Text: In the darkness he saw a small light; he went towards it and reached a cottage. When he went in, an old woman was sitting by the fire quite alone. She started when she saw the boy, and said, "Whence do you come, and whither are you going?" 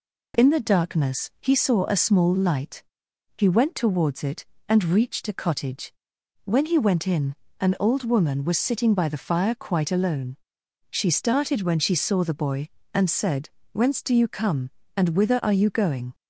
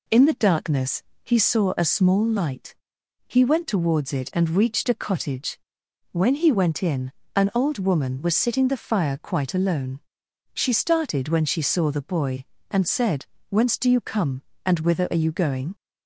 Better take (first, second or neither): first